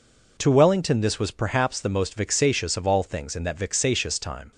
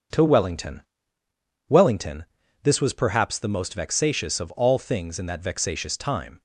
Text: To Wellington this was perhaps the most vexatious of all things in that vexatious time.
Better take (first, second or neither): first